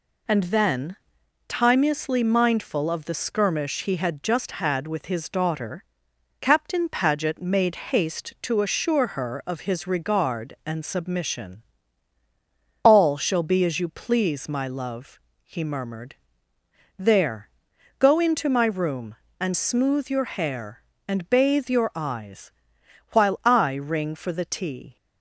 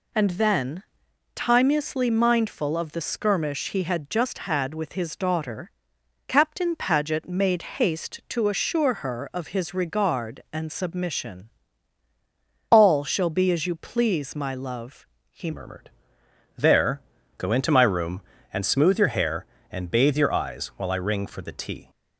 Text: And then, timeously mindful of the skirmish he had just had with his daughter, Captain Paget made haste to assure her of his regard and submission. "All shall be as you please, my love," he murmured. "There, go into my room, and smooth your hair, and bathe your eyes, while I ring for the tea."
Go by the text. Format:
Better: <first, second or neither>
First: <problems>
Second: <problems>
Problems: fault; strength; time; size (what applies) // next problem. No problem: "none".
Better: first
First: none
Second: changes voice at "murmured"; from 15.5 s on; 6.3 s long